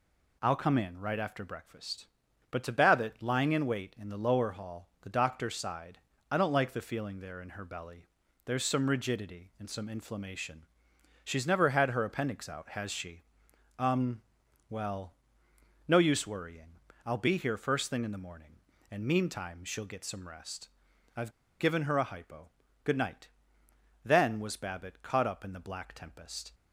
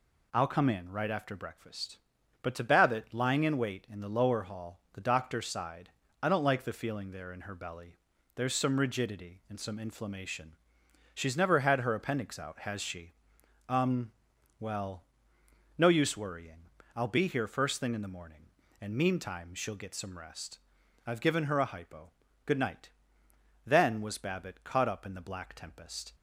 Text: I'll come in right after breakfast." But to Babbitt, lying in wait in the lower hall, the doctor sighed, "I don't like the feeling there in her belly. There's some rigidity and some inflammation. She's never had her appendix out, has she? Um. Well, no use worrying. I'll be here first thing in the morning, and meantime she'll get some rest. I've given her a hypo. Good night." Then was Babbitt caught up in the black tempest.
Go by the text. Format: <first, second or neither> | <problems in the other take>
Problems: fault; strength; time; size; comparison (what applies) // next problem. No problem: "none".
second | pauses between "I've" and "given"; slight; at 21.3 s; 0.29 s long